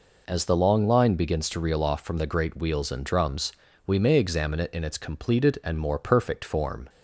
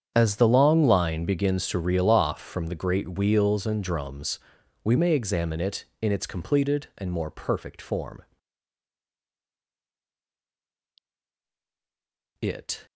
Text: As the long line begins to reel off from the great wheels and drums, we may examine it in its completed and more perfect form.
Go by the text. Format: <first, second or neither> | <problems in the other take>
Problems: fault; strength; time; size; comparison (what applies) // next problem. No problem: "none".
first | starts louder than the rest; strong; until 1.1 s; 8 dB // goes on to say "It"; slight; from 12.4 s on; 0.44 s long